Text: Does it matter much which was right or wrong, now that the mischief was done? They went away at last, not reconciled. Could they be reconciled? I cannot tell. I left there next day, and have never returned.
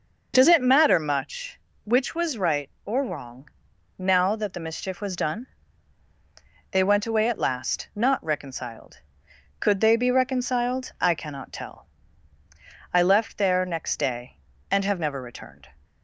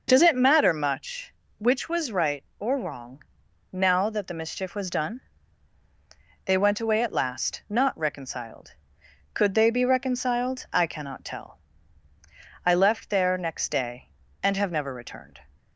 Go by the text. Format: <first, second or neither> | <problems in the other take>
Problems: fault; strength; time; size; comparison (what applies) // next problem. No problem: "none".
neither | none